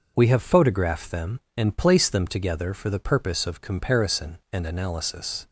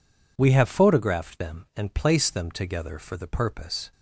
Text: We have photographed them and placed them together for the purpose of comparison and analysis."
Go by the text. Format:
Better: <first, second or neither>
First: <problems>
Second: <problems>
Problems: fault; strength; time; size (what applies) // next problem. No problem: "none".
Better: first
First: none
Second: stops before "of comparison and analysis"; at 3.9 s